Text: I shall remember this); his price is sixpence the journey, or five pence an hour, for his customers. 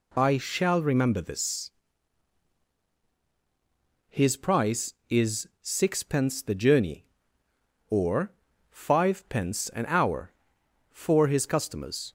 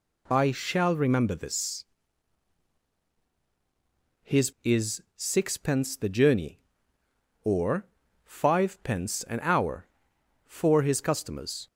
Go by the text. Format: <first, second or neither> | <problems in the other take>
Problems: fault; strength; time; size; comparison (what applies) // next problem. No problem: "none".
first | skips "price"; at 4.5 s // pauses between "or" and "five"; at 7.8 s; 0.38 s long; also in the first